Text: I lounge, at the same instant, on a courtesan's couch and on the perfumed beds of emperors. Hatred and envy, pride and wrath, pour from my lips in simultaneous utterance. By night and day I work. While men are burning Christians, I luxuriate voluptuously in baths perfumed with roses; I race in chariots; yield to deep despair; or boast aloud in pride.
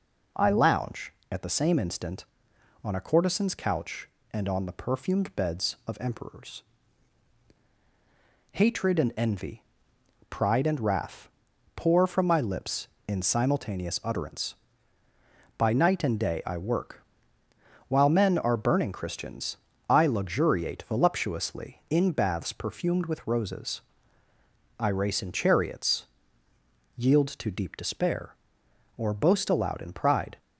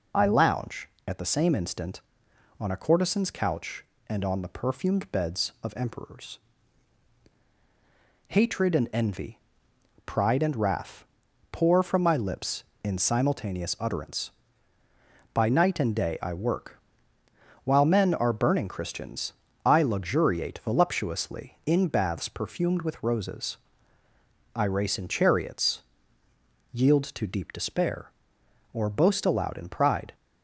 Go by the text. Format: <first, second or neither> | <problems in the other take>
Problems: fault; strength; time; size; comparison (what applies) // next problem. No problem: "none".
first | loses the start of "I"; at 0.1 s; 25 ms